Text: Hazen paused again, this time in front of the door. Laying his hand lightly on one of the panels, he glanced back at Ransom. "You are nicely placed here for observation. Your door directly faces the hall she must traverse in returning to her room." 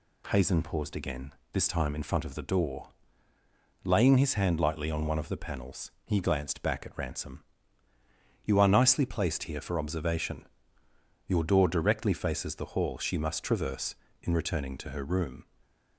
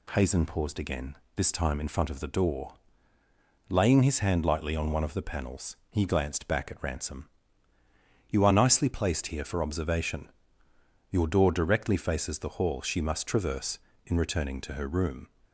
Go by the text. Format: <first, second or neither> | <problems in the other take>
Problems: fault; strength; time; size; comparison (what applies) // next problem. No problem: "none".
neither | none